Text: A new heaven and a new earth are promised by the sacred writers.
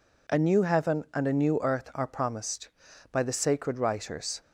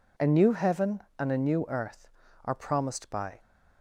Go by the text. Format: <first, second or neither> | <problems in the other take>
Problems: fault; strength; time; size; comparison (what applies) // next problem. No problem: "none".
first | stops before "the sacred writers"; at 3.4 s